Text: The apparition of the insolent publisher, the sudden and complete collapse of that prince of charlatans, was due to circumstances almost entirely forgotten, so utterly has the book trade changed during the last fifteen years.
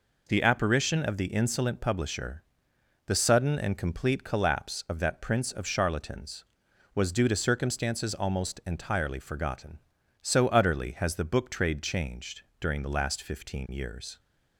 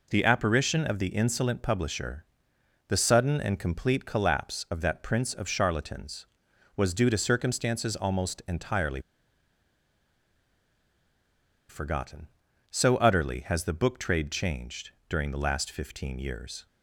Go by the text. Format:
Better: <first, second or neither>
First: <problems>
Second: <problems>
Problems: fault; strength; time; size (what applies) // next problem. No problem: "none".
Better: first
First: pauses between "changed" and "during"; slight; at 12.4 s; 0.18 s long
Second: pauses between "entirely" and "forgotten"; strong; at 9.0 s; 2.6 s long // pauses between "changed" and "during"; slight; at 14.9 s; 0.18 s long